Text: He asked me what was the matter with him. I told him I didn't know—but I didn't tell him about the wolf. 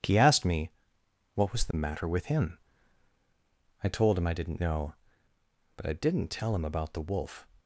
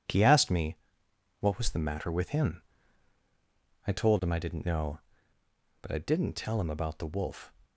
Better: neither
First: pauses between "me" and "what"; noticeable; at 0.7 s; 0.64 s long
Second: pauses between "me" and "what"; noticeable; at 0.7 s; 0.64 s long

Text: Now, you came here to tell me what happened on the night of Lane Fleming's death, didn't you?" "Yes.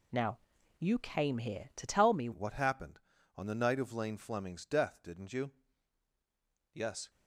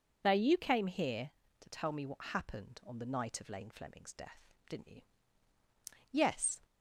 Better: second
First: changes voice at "what"; from 2.3 s on; 4.7 s long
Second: none

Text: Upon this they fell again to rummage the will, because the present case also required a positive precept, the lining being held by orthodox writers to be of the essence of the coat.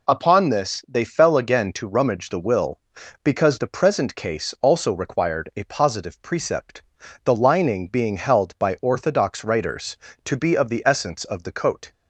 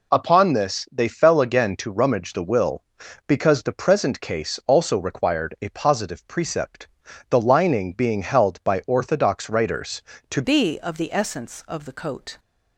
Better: first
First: none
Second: changes voice at "be"; from 10.4 s on; 1.9 s long

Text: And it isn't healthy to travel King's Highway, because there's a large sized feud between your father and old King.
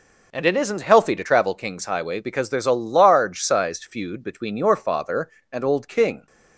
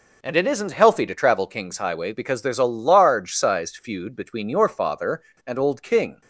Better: neither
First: none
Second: none

